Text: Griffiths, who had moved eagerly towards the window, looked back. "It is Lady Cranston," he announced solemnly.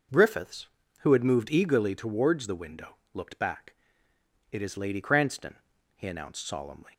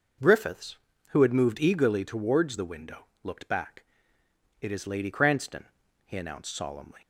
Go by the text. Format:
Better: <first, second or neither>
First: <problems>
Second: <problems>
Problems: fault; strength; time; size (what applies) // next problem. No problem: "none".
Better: neither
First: none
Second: none